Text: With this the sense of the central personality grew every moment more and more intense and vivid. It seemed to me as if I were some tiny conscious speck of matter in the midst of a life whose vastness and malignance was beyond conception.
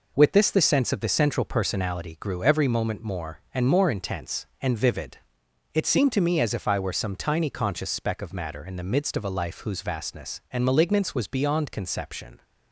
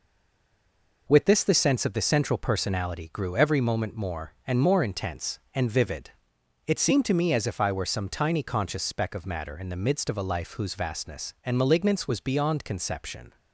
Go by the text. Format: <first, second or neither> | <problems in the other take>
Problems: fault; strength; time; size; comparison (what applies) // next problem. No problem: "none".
first | stays silent before the first word; until 1.0 s; 1.0 s long